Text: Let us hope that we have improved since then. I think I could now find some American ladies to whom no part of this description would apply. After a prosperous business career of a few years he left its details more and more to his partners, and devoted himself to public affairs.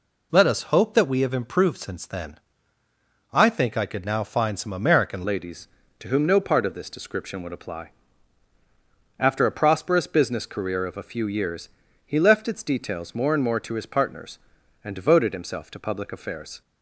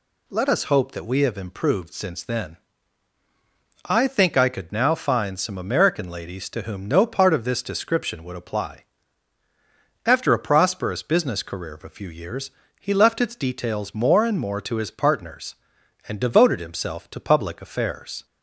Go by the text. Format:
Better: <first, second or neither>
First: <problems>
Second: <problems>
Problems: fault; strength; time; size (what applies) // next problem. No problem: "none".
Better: second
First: changes voice at "ladies"; from 5.2 s on; 11.4 s long // pauses between "years" and "he"; slight; at 11.6 s; 0.36 s long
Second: pauses between "years" and "he"; slight; at 12.4 s; 0.30 s long